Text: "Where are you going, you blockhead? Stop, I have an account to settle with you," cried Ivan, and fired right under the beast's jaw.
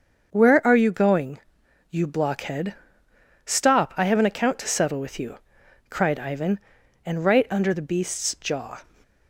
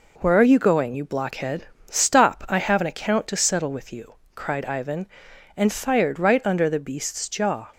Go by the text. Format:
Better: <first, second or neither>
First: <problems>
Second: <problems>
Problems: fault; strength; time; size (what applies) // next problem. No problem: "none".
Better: second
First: starts louder than the rest; until 1.3 s; 6.5 dB // skips "fired"; at 7.2 s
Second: none